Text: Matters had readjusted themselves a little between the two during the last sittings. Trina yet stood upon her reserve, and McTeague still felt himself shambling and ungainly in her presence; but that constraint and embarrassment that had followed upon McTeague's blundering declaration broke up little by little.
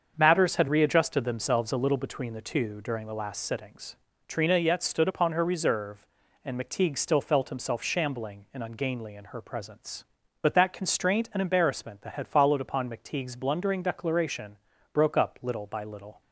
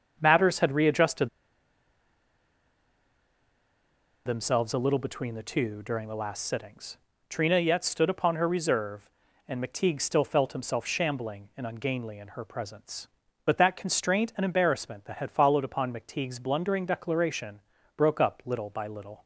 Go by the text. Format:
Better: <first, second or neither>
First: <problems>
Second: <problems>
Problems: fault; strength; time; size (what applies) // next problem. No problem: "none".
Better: first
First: starts louder than the rest; until 1.1 s; 6.5 dB // pauses between "declaration" and "broke"; slight; at 14.5 s; 0.36 s long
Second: starts louder than the rest; until 1.2 s; 6.5 dB // pauses between "readjusted" and "themselves"; strong; at 1.2 s; 2.9 s long // pauses between "declaration" and "broke"; slight; at 17.5 s; 0.36 s long